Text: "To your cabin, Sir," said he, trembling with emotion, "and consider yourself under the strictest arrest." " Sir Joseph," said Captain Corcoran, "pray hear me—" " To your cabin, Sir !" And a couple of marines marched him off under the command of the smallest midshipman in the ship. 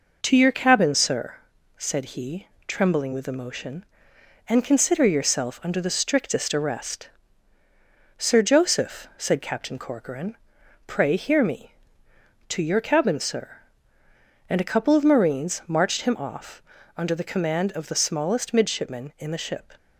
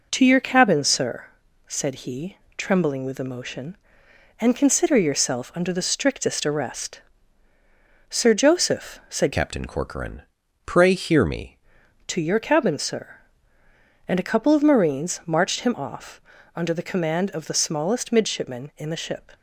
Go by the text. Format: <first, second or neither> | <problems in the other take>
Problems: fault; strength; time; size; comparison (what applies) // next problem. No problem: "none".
first | changes voice from "Captain" to "me"; from 9.3 to 11.5 s; 2.2 s long // pauses between "off" and "under"; slight; at 16.2 s; 0.34 s long; slight in the first